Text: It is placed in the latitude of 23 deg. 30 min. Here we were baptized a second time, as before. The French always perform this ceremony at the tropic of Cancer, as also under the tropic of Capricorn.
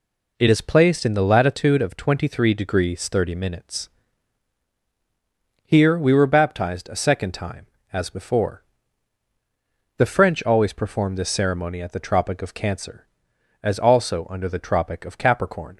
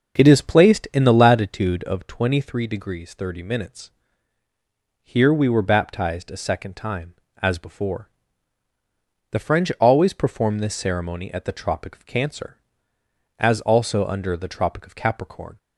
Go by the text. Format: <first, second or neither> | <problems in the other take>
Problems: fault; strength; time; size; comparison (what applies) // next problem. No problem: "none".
first | starts louder than the rest; until 1.8 s; 6.5 dB